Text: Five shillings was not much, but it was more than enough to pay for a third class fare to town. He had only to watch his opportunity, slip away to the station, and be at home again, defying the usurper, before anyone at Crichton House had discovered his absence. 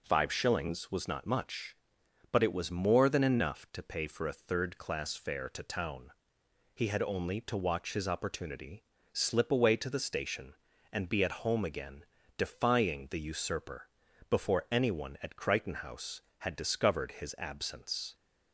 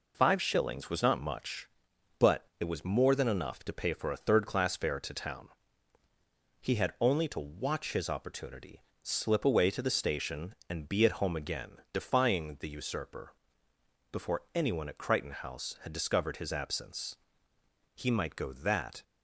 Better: first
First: none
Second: pauses between "but" and "it"; slight; at 2.4 s; 0.16 s long // goes on to say "He might go that"; noticeable; from 17.9 s on; 1.0 s long

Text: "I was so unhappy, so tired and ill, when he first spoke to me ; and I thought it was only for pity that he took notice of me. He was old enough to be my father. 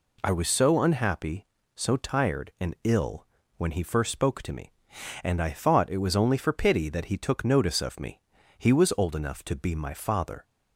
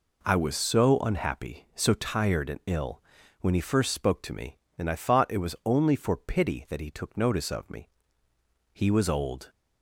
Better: first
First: none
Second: stops before "enough to be my father"; at 9.4 s

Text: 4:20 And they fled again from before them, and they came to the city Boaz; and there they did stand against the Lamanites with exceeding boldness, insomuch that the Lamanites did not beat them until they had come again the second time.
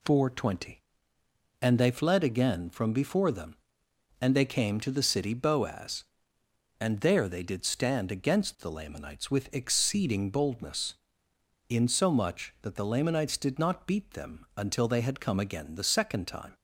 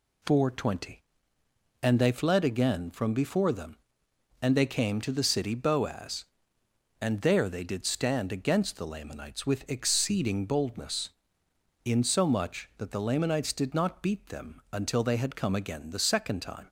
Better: neither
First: none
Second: none

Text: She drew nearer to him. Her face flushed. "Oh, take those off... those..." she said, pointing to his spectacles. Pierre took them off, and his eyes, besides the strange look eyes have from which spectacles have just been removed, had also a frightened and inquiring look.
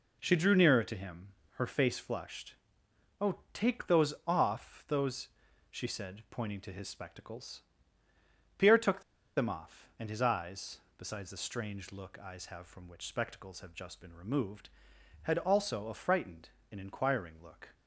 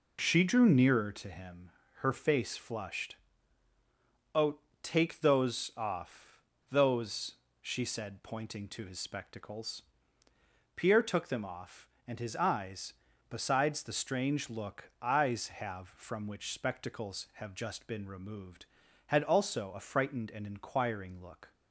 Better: second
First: pauses between "took" and "them"; at 9.0 s; 0.36 s long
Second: none

